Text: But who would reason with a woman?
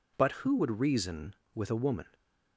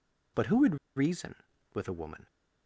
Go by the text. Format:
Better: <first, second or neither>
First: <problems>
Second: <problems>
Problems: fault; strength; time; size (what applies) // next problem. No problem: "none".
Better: first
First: none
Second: pauses between "would" and "reason"; slight; at 0.7 s; 0.20 s long